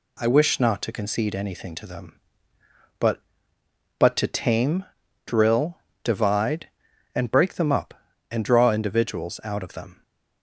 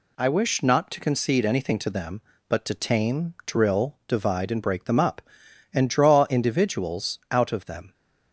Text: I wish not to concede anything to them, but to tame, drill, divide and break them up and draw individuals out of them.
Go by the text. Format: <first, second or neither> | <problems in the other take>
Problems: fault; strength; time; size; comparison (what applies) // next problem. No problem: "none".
second | says "but" twice; at 3.9 s